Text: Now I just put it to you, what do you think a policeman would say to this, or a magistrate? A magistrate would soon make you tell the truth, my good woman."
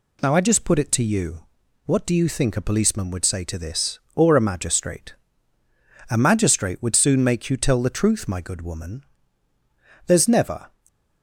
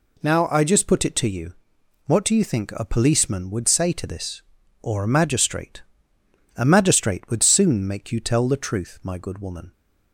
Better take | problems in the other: second | goes on to say "There's never"; noticeable; from 10.0 s on; 0.62 s long

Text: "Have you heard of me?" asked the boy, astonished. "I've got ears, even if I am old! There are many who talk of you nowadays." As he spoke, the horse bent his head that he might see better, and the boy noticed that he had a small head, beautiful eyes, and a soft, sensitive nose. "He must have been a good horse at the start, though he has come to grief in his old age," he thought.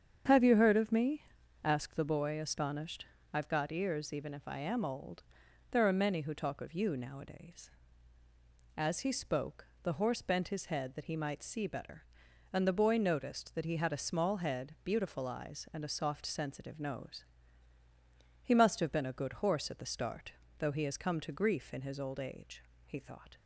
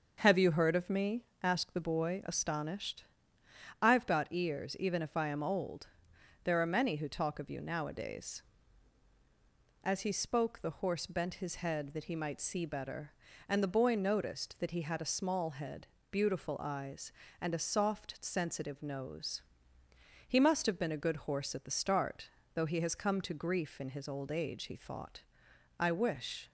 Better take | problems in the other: first | starts louder than the rest; until 1.2 s; 6.5 dB; strong in the first // goes on to say "I wish"; noticeable; from 25.7 s on; 0.72 s long

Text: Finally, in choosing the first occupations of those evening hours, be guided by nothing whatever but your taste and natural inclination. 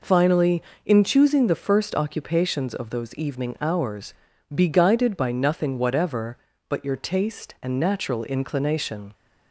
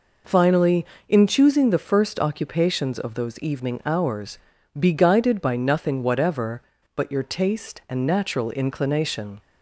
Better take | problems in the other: neither | none

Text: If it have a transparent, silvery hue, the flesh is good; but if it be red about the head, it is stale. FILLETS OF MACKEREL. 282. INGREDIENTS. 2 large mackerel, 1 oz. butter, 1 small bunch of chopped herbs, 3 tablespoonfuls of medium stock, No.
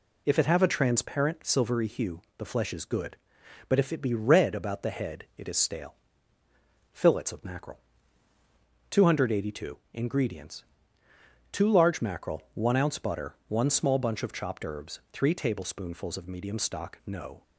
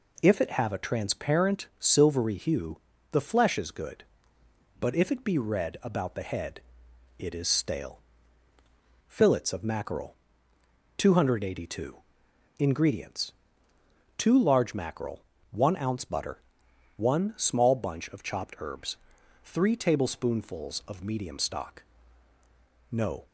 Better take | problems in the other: neither | none

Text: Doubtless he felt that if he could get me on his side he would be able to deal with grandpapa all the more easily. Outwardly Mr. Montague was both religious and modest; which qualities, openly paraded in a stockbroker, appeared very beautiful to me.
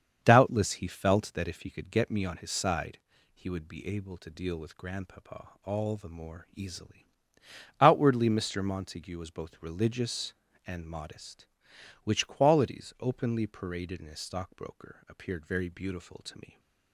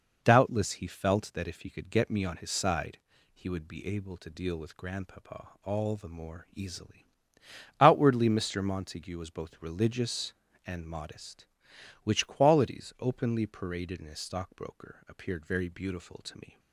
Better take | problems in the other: second | starts louder than the rest; strong; until 1.9 s; 7 dB // pauses between "side" and "he"; slight; at 2.9 s; 0.36 s long; slight in the second // pauses between "grandpapa" and "all"; slight; at 5.4 s; 0.16 s long; slight in the second

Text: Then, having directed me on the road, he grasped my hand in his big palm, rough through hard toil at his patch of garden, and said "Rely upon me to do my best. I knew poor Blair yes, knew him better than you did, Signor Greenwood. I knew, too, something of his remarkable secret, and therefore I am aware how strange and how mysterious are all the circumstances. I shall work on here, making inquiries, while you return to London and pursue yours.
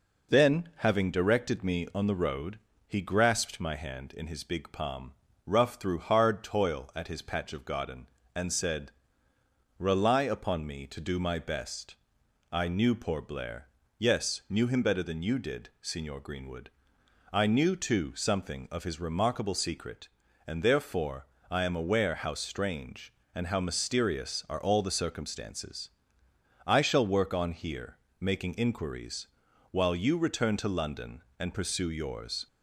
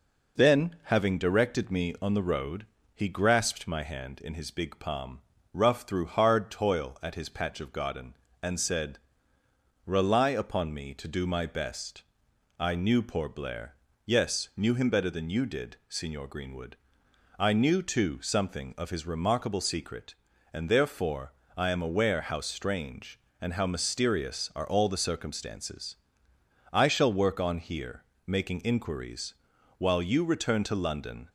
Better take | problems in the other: first | pauses between "said" and "Rely"; noticeable; at 8.9 s; 0.88 s long; noticeable in the first // pauses between "Blair" and "yes"; slight; at 13.7 s; 0.28 s long; slight in the first // pauses between "therefore" and "I"; slight; at 21.3 s; 0.24 s long; slight in the first // stops before "and pursue yours"; at 31.2 s

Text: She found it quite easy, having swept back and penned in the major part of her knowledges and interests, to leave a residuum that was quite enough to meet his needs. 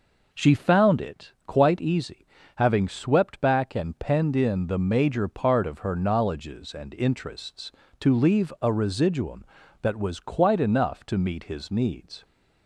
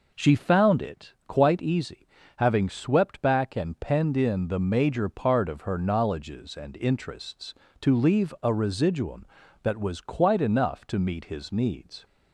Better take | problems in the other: neither | pauses between "it" and "quite"; slight; the same in both

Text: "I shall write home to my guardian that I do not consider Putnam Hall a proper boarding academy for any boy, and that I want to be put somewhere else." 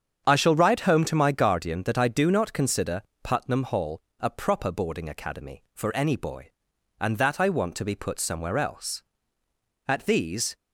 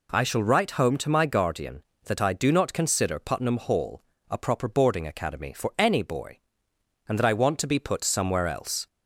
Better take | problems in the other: second | starts louder than the rest; strong; until 1.2 s; 8 dB // pauses between "consider" and "Putnam"; slight; at 3.0 s; 0.22 s long // pauses between "Hall" and "a"; slight; at 4.0 s; 0.18 s long; slight in the second // goes on to say "At these"; noticeable; from 9.8 s on; 0.68 s long

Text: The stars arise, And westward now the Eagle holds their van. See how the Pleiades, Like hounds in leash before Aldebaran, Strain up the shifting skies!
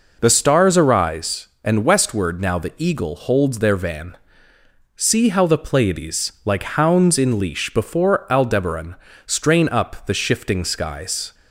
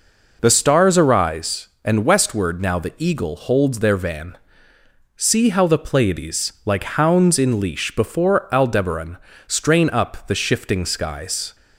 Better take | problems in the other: neither | none

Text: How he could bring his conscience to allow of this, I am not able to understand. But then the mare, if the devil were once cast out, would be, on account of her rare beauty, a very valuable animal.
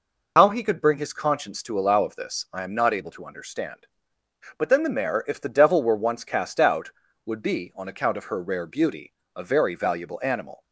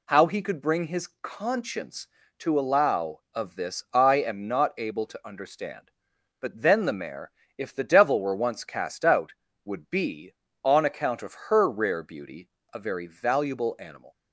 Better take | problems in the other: second | loses the start of "How"; at 0.3 s; 60 ms

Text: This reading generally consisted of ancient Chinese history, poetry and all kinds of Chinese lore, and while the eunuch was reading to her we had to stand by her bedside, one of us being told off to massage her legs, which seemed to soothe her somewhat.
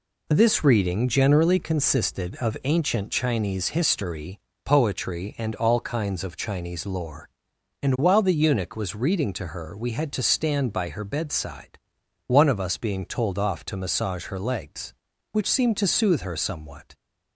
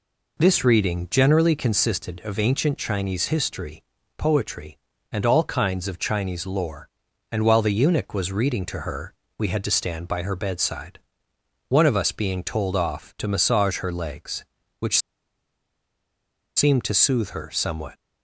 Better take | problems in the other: first | pauses between "her" and "we"; slight; at 9.1 s; 0.22 s long // pauses between "which" and "seemed"; strong; at 14.9 s; 1.5 s long

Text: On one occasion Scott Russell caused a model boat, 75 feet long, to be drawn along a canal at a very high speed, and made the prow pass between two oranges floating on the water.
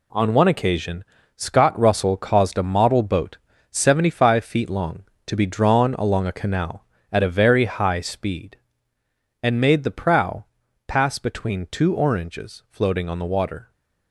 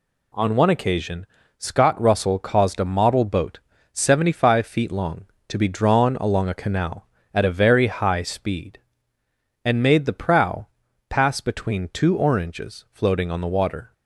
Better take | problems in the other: second | gets quieter; strong; throughout; 7.5 dB // pauses between "occasion" and "Scott"; slight; at 1.0 s; 0.32 s long; slight in the second // pauses between "prow" and "pass"; at 10.4 s; 0.44 s long; also in the second

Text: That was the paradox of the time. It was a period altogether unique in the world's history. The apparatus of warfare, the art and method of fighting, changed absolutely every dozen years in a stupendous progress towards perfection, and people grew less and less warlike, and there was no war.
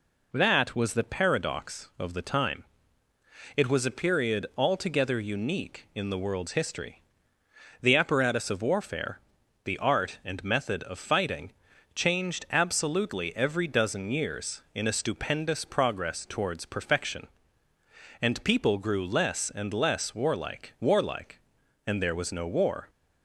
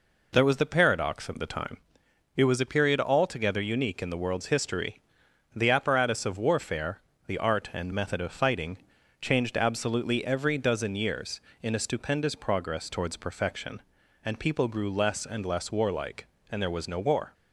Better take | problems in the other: second | says "warlike" twice; at 20.7 s

